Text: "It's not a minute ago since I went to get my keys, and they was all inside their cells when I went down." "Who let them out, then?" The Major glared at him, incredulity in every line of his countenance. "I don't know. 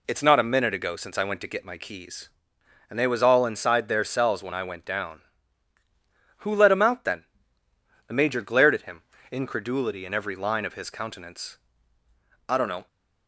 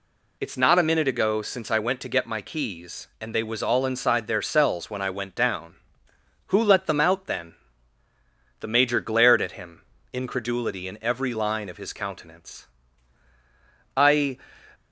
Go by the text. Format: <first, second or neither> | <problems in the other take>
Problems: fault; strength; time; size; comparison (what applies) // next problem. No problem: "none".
first | stops before "don't know"; at 14.7 s